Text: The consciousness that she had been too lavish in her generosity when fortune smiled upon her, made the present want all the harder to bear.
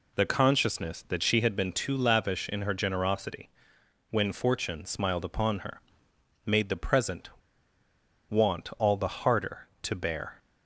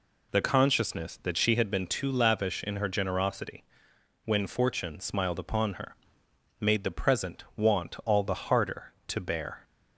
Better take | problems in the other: second | pauses between "generosity" and "when"; noticeable; at 3.4 s; 0.60 s long; noticeable in the second // pauses between "present" and "want"; at 7.2 s; 0.99 s long

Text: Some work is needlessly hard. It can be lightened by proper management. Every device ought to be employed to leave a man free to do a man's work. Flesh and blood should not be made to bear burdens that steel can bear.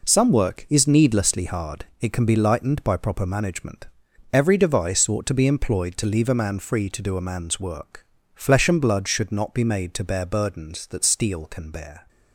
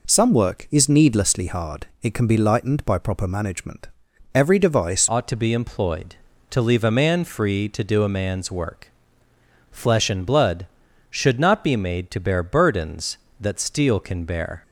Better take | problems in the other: first | changes voice at "ought"; from 5.0 s on; 9.6 s long

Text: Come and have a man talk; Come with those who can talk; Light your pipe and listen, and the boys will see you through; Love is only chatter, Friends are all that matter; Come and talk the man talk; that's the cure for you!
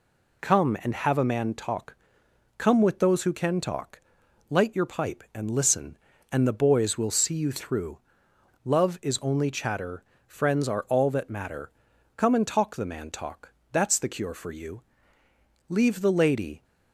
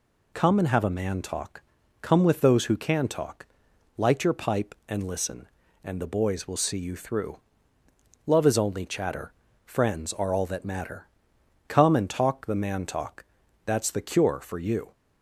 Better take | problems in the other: second | goes on to say "Leave the lady"; noticeable; from 15.6 s on; 0.96 s long

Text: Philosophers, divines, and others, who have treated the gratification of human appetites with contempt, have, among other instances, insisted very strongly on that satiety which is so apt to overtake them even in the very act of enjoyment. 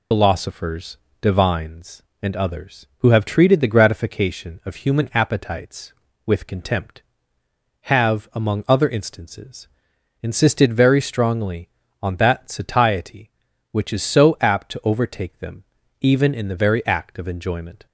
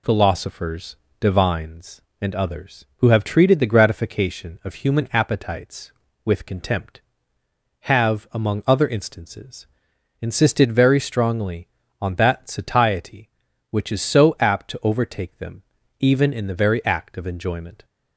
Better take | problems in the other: second | loses the start of "Philosophers"; at 0.1 s; 55 ms // pauses between "them" and "even"; slight; at 15.6 s; 0.36 s long; slight in the second

